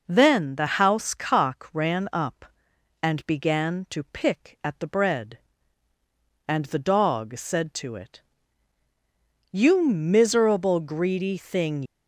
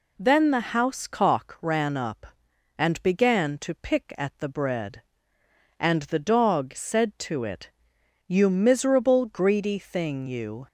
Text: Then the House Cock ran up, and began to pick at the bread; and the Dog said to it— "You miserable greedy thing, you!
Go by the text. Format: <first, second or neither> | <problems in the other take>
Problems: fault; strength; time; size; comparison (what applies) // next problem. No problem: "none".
second | stops before "you"; at 11.8 s